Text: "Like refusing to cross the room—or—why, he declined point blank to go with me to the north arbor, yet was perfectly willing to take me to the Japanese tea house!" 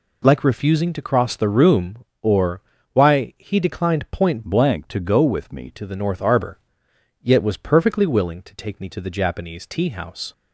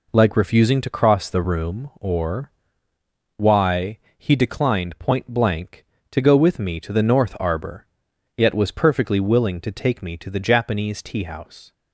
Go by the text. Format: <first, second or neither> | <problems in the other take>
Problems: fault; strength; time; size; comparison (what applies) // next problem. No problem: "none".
second | changes voice from "blank" to "me"; from 4.4 to 5.7 s; 1.3 s long